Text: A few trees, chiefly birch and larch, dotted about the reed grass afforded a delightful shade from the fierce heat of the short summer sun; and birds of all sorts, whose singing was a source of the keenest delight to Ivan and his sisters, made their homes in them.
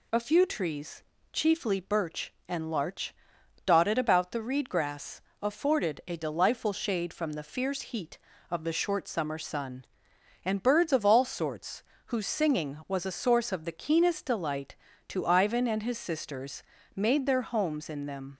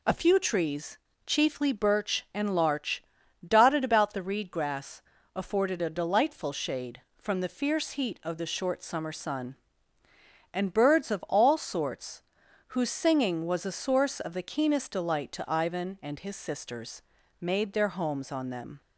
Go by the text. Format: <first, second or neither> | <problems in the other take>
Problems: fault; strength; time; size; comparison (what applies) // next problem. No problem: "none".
first | pauses between "grass" and "afforded"; slight; at 5.0 s; 0.32 s long; slight in the first // says "on" for "in"; at 18.3 s